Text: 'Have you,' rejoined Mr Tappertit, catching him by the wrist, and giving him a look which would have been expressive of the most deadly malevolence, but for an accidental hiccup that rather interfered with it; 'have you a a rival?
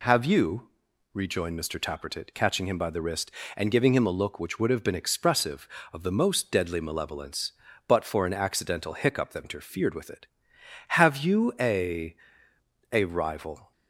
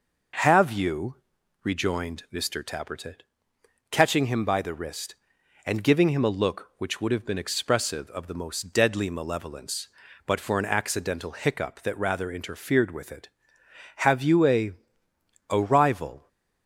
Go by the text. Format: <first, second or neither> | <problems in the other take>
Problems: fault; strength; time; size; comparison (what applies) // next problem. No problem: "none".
second | skips "rather"; at 9.4 s // pauses between "a" and "a"; noticeable; at 12.1 s; 0.76 s long; noticeable in the second